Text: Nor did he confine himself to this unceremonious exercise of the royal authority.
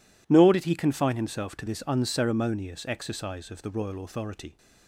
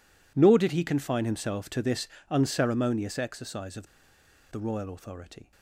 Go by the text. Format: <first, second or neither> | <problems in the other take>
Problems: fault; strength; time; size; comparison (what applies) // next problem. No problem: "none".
first | pauses between "this" and "unceremonious"; slight; at 2.0 s; 0.22 s long // pauses between "of" and "the"; noticeable; at 3.8 s; 0.64 s long